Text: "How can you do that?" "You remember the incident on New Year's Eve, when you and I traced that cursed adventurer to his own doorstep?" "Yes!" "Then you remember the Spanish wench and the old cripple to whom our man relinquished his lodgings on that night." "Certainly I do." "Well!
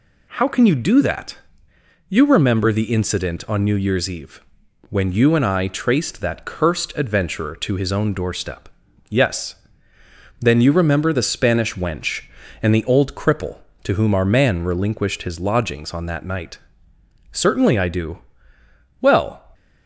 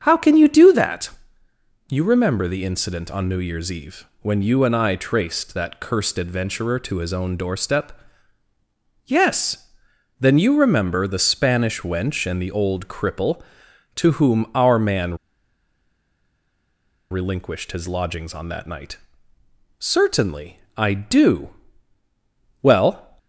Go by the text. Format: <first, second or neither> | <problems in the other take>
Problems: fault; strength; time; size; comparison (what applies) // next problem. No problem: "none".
first | starts louder than the rest; strong; until 1.0 s; 7.5 dB // pauses between "man" and "relinquished"; strong; at 15.1 s; 1.9 s long // pauses between "Certainly" and "I"; slight; at 20.5 s; 0.16 s long